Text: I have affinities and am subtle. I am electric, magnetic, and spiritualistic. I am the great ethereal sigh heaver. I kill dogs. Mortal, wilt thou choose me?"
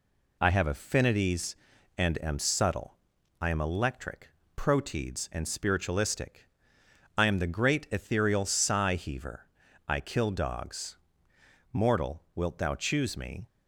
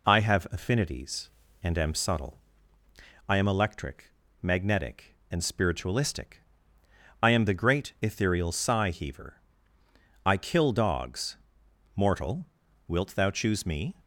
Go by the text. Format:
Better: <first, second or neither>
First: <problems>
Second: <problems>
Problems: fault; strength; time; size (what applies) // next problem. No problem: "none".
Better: second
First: says "proteids" for "magnetic"; at 4.5 s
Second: none